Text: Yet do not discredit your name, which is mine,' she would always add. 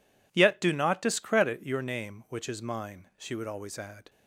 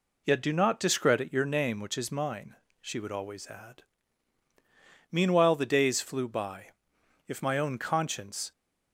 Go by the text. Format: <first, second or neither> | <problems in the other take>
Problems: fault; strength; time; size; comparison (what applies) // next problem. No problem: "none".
first | goes on to say "Meanwhile the days flew by If my own conscience"; strong; from 5.0 s on; 3.4 s long